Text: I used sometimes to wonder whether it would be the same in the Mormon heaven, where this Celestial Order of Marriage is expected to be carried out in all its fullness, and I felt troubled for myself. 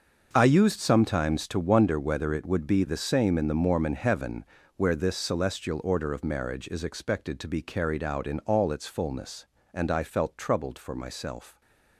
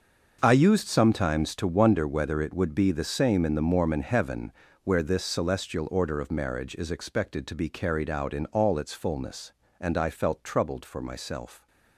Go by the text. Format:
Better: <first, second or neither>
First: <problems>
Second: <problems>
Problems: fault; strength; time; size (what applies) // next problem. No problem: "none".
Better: neither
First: starts louder than the rest; until 1.3 s; 6 dB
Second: starts louder than the rest; until 1.4 s; 6 dB